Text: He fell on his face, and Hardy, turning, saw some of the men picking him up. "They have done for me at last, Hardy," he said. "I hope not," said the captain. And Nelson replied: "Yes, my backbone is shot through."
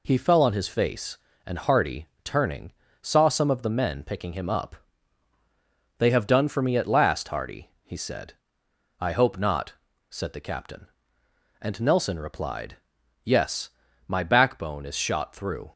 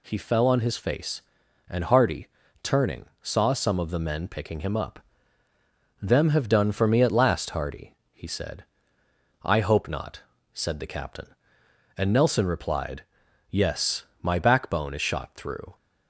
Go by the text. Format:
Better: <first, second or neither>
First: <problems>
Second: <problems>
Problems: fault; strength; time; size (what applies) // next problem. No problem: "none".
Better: first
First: none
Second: says "Them" for "They"; at 5.9 s